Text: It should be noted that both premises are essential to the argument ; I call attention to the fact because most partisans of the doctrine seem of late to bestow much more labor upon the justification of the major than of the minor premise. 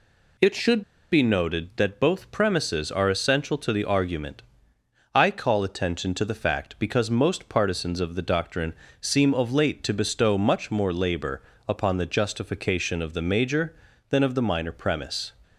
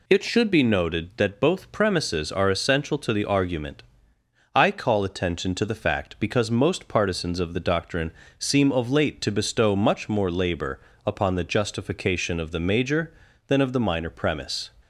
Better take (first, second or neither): second